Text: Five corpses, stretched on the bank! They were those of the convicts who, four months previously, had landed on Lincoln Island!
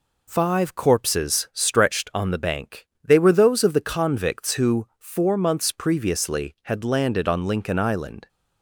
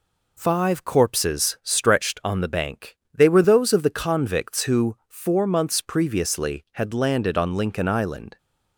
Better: neither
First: none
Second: none

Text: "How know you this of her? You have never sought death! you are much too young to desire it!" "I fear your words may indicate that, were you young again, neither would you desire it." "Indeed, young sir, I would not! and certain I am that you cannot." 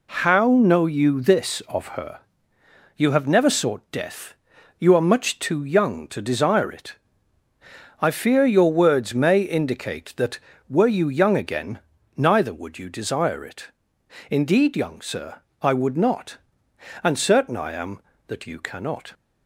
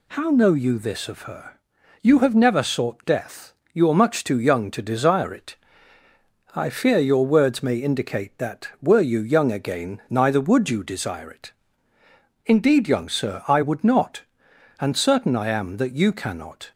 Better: neither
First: none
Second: none

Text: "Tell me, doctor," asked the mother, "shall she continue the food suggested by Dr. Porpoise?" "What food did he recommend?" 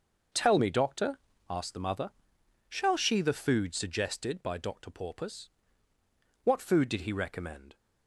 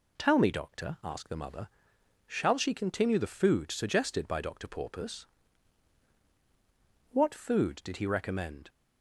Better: second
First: starts louder than the rest; noticeable; until 1.6 s; 6 dB // skips "continue"; at 3.2 s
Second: none

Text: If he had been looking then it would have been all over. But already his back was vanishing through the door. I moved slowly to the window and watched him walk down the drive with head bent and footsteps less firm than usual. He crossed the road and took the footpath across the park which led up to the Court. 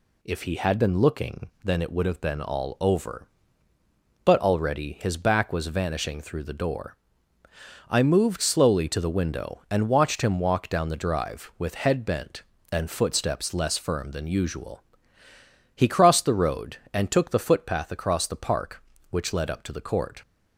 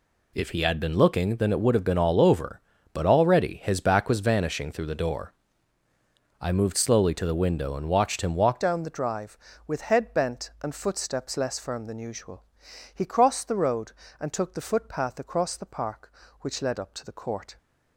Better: first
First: none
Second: changes voice at "down"; from 8.5 s on; 9.0 s long

